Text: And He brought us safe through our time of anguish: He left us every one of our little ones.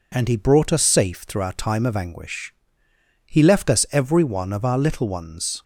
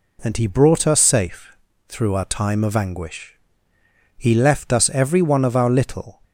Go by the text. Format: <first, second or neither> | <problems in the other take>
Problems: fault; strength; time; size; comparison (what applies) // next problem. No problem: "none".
first | pauses between "safe" and "through"; slight; at 1.5 s; 0.32 s long // stops before "ones"; at 6.2 s